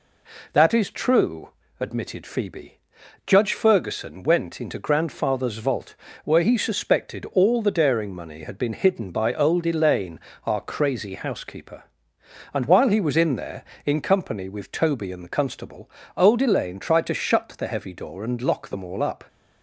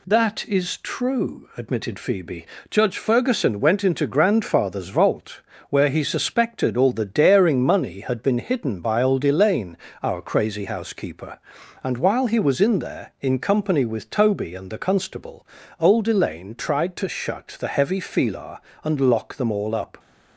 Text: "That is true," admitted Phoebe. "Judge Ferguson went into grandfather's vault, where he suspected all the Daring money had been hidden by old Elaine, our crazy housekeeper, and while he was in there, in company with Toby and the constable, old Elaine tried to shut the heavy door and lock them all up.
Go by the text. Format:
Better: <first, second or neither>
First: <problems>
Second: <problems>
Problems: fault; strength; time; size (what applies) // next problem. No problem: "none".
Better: first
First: none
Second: says "filar" for "door"; at 18.0 s